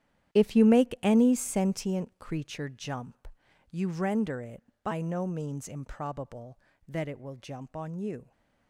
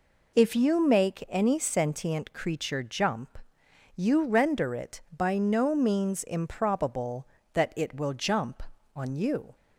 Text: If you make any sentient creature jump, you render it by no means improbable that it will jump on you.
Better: second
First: gets quieter; strong; throughout; 13 dB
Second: none

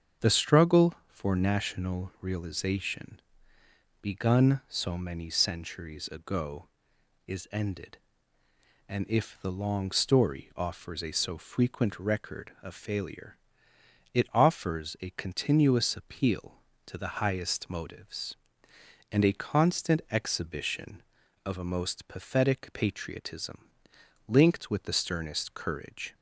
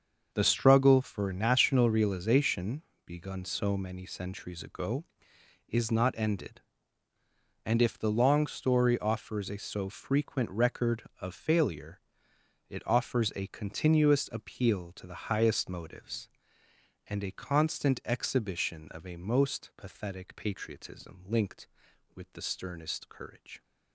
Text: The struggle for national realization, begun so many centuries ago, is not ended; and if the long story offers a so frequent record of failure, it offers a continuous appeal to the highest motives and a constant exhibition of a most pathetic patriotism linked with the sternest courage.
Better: second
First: starts louder than the rest; strong; until 1.3 s; 7.5 dB // skips "not"; at 7.4 s // pauses between "patriotism" and "linked"; noticeable; at 23.6 s; 0.60 s long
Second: starts louder than the rest; until 1.3 s; 6.5 dB

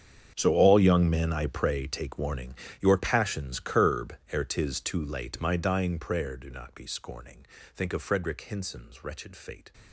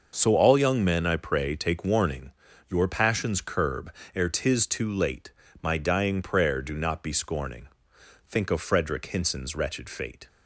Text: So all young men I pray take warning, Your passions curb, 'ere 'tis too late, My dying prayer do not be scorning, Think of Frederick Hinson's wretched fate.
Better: second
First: gets quieter; strong; throughout; 17 dB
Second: none

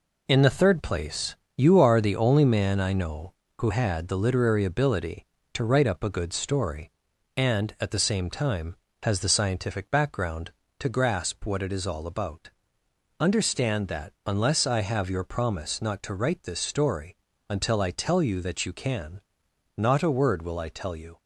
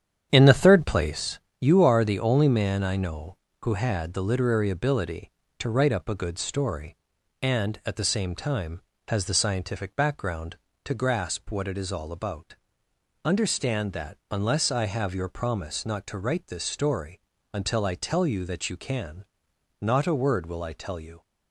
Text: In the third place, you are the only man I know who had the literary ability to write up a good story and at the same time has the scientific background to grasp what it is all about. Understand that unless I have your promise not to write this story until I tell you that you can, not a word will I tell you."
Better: first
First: pauses between "story" and "until"; slight; at 17.1 s; 0.34 s long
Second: starts louder than the rest; strong; until 1.2 s; 9 dB // pauses between "story" and "until"; slight; at 17.2 s; 0.34 s long

